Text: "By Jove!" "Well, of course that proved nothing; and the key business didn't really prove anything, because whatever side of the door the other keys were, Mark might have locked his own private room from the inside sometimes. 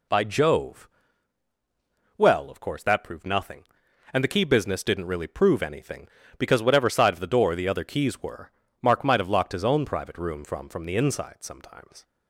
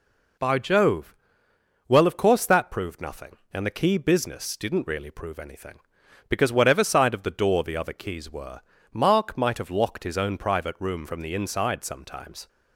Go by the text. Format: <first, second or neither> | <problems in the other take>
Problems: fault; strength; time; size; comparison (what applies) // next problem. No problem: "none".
second | says "from" twice; at 10.6 s